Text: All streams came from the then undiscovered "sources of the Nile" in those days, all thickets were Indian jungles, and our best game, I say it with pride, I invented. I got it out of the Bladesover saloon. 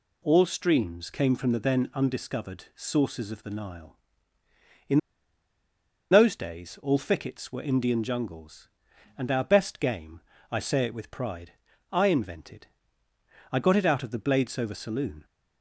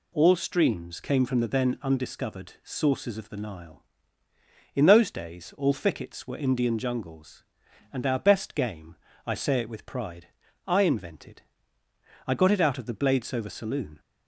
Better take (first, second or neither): second